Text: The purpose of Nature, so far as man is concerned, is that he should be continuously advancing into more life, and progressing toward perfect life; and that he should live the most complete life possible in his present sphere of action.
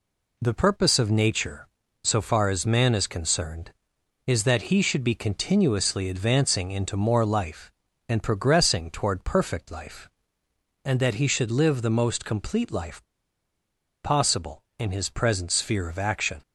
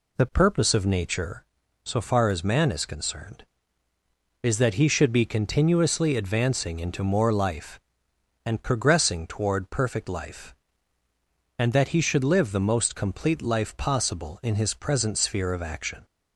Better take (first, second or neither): second